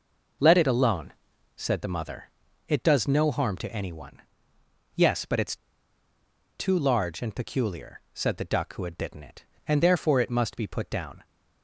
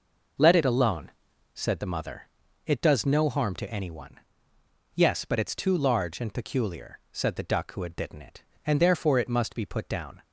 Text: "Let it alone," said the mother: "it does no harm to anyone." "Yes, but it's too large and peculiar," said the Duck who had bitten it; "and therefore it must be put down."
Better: second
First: pauses between "it's" and "too"; at 5.5 s; 1.0 s long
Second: none

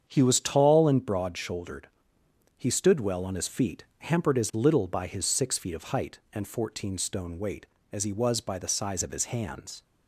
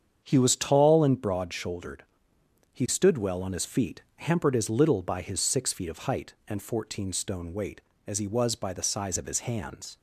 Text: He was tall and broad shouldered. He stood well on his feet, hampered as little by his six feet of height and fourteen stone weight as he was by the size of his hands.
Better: neither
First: starts louder than the rest; strong; until 1.0 s; 7.5 dB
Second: starts louder than the rest; strong; until 1.2 s; 7.5 dB

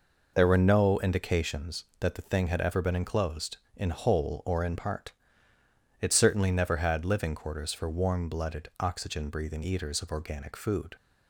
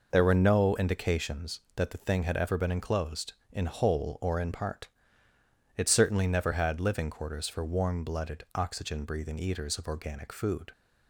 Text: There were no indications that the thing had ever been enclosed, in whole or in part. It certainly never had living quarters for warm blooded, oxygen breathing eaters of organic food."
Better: neither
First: none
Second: none

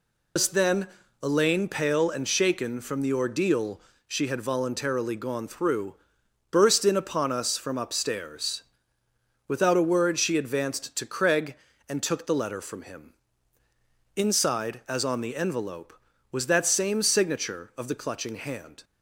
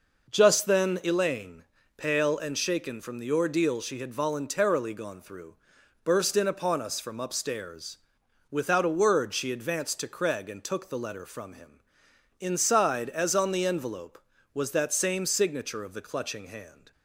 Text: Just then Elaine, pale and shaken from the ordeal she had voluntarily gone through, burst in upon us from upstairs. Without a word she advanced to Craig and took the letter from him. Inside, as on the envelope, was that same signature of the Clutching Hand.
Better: second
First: loses the start of "Just"; at 0.3 s; 170 ms // pauses between "then" and "Elaine"; slight; at 0.8 s; 0.34 s long // pauses between "ordeal" and "she"; slight; at 3.7 s; 0.28 s long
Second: none

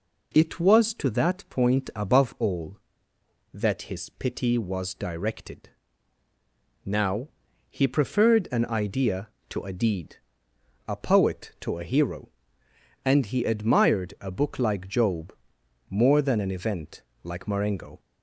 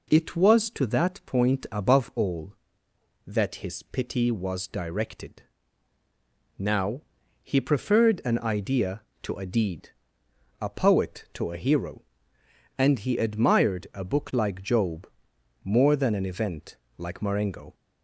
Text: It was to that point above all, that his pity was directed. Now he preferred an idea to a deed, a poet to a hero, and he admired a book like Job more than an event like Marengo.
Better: neither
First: pauses between "Now" and "he"; at 7.2 s; 0.42 s long // pauses between "Job" and "more"; noticeable; at 15.3 s; 0.56 s long // pauses between "event" and "like"; slight; at 17.0 s; 0.22 s long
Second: pauses between "Now" and "he"; at 7.0 s; 0.42 s long // pauses between "Job" and "more"; noticeable; at 15.0 s; 0.56 s long // pauses between "event" and "like"; slight; at 16.7 s; 0.22 s long

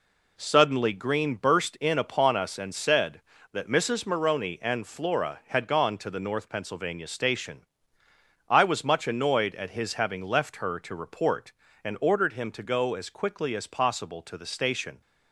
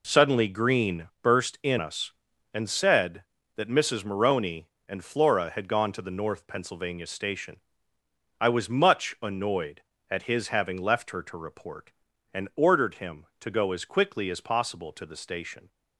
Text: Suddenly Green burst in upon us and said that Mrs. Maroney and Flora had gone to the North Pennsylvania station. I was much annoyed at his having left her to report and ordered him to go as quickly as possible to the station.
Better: first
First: none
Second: pauses between "Green" and "burst"; slight; at 1.0 s; 0.16 s long // skips "upon"; at 1.7 s

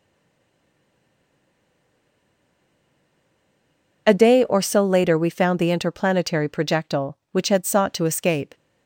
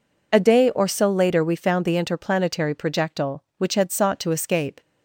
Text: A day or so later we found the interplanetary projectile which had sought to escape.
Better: second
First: stays silent before the first word; strong; until 4.0 s; 4.0 s long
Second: none

